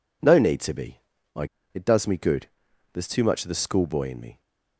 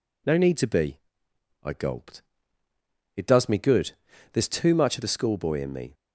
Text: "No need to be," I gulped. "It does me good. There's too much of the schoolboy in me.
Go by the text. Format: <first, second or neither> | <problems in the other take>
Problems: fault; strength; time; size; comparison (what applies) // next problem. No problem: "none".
second | skips "gulped"; at 1.6 s